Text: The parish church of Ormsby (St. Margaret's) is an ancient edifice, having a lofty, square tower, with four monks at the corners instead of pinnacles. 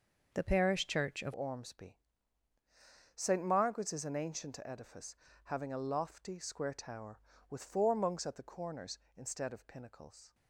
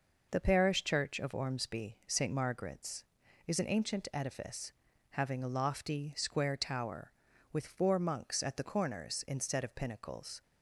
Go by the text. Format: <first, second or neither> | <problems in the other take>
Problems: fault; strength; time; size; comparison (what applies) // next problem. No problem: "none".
second | changes voice at "Ormsby"; from 1.3 s on; 9.0 s long